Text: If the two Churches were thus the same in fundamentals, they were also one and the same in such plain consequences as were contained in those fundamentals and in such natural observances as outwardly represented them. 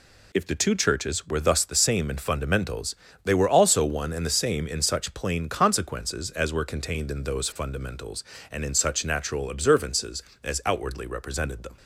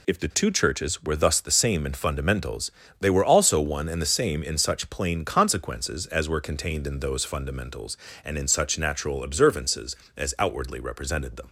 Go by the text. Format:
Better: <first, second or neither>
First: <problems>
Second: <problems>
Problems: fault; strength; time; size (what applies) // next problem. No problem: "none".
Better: neither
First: none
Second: none